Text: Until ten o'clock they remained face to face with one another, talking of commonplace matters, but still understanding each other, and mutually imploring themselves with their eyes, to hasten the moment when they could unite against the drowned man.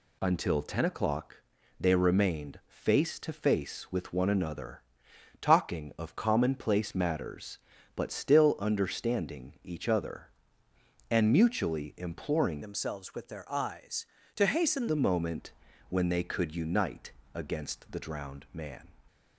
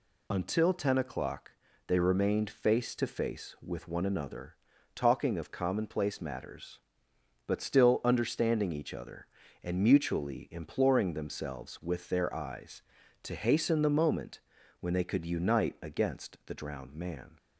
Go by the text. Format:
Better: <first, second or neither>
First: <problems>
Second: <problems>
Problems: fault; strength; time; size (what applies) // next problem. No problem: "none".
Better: second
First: pauses between "o'clock" and "they"; at 1.3 s; 0.42 s long // changes voice from "themselves" to "hasten"; from 12.6 to 14.8 s; 2.2 s long // pauses between "moment" and "when"; at 15.5 s; 0.38 s long // pauses between "unite" and "against"; slight; at 17.1 s; 0.24 s long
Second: pauses between "o'clock" and "they"; slight; at 1.5 s; 0.36 s long // pauses between "moment" and "when"; at 14.4 s; 0.40 s long